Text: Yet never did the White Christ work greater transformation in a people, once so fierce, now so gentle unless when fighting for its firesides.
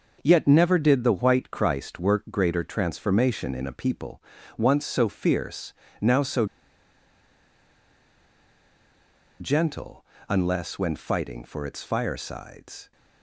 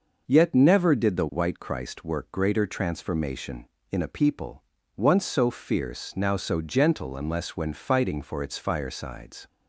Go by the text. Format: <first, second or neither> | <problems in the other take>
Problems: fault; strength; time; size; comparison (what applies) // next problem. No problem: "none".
second | pauses between "so" and "gentle"; strong; at 6.4 s; 2.9 s long // pauses between "gentle" and "unless"; slight; at 10.0 s; 0.24 s long